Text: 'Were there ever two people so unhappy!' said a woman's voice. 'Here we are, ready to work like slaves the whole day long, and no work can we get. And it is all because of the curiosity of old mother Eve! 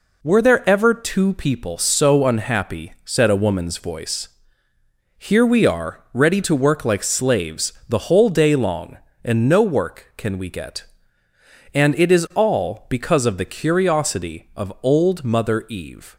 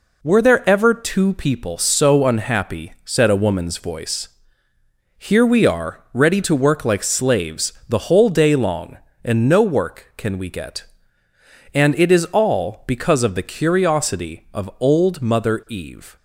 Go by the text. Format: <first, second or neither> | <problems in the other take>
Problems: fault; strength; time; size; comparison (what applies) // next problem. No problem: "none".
neither | pauses between "slaves" and "the"; slight; the same in both